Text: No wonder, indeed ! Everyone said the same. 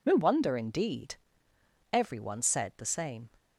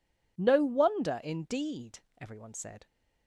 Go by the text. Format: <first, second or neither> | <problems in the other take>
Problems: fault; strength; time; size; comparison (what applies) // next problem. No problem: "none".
first | stops before "the same"; at 2.8 s